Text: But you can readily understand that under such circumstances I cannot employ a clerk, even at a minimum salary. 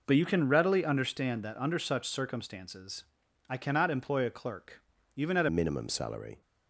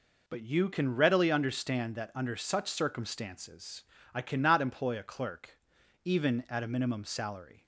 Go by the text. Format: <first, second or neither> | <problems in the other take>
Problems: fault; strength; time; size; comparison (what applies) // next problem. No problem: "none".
second | pauses between "circumstances" and "I"; noticeable; at 3.0 s; 0.46 s long; slight in the second // changes voice at "minimum"; from 5.4 s on; 1.0 s long